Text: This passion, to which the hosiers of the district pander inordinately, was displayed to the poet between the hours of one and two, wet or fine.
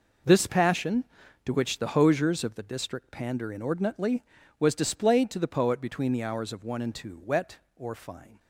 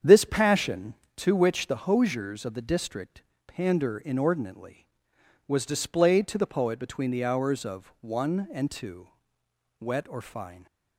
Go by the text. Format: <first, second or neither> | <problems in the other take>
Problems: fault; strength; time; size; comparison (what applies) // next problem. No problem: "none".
first | starts louder than the rest; strong; until 1.2 s; 8 dB // pauses between "district" and "pander"; slight; at 3.2 s; 0.24 s long